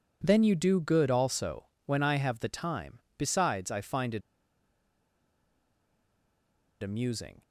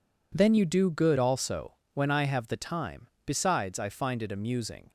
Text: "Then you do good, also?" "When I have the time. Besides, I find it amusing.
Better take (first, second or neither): second